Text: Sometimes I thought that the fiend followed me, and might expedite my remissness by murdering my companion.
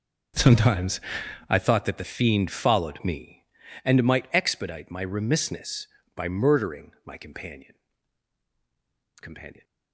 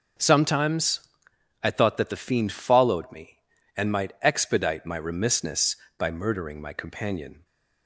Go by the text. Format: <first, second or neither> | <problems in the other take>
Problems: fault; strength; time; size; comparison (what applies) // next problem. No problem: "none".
second | pauses between "Sometimes" and "I"; noticeable; at 0.9 s; 0.50 s long; noticeable in the second // says "companion" twice; at 9.2 s